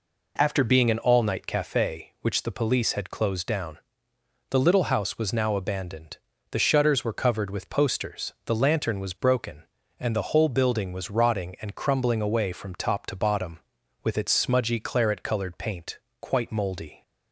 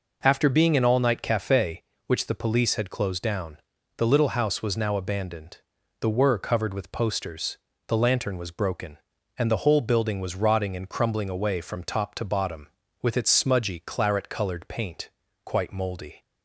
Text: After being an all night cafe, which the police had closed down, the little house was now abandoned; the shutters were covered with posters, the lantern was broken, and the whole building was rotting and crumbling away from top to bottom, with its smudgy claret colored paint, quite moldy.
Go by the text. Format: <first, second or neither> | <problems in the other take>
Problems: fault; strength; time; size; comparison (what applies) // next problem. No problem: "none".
first | skips "shutters"; at 6.1 s